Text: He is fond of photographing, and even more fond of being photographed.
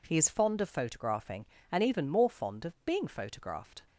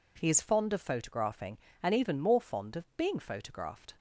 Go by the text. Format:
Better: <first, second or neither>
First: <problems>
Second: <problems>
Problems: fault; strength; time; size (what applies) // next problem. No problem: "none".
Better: neither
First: none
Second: none